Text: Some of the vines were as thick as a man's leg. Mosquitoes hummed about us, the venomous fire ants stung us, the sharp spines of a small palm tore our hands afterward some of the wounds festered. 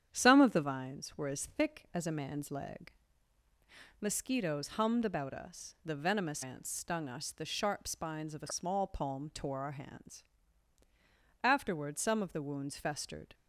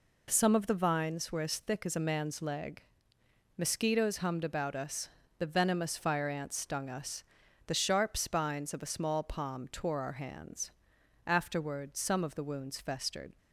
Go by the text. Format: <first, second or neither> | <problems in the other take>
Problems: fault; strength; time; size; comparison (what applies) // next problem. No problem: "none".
second | starts louder than the rest; strong; until 1.1 s; 9 dB // skips "fire"; at 6.4 s // pauses between "hands" and "afterward"; at 10.2 s; 1.2 s long; noticeable in the second